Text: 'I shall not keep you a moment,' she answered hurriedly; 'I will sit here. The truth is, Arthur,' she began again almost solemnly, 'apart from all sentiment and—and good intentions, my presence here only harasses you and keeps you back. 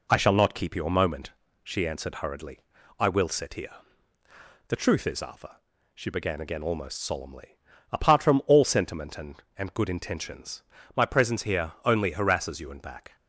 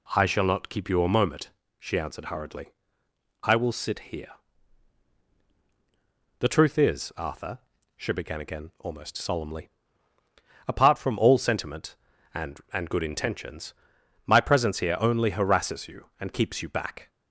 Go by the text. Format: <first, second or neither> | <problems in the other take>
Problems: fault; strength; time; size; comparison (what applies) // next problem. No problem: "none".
second | skips "keeps you"; at 12.8 s